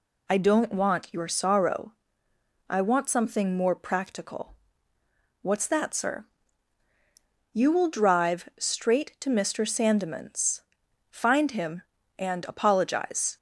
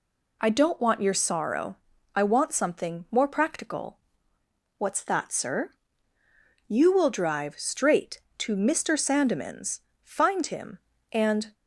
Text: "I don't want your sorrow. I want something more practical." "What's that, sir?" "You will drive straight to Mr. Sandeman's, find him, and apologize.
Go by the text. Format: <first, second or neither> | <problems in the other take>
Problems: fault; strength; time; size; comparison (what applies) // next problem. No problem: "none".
first | stops before "apologize"; at 11.5 s